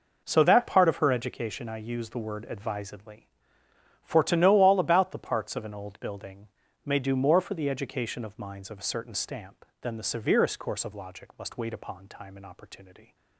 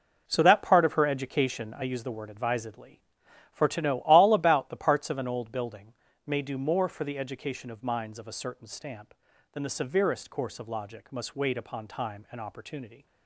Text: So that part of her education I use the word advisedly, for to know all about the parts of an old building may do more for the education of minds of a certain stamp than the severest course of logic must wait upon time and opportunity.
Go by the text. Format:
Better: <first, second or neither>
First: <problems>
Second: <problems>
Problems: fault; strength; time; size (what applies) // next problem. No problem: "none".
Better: neither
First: pauses between "building" and "may"; at 6.4 s; 0.38 s long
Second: pauses between "building" and "may"; slight; at 5.9 s; 0.32 s long